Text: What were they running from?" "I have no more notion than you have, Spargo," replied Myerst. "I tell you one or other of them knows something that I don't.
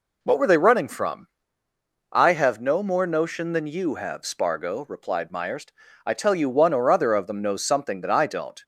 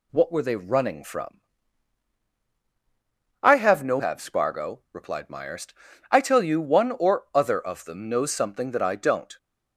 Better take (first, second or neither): first